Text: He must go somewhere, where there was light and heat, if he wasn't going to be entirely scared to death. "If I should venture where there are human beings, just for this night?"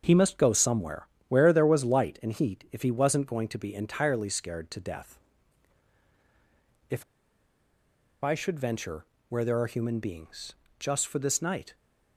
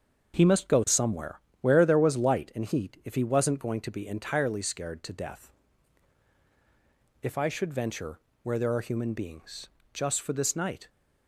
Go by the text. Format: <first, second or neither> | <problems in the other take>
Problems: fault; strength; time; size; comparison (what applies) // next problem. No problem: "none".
second | starts louder than the rest; until 1.0 s; 6.5 dB; also in the second // pauses between "If" and "I"; at 7.0 s; 1.2 s long // pauses between "venture" and "where"; slight; at 9.0 s; 0.24 s long; slight in the second